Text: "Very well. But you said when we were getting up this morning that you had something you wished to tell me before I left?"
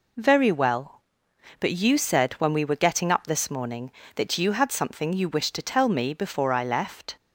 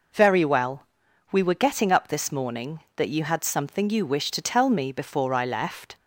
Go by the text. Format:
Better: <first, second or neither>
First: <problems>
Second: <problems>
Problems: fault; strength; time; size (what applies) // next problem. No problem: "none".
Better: first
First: none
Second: skips "But you said when"; at 1.0 s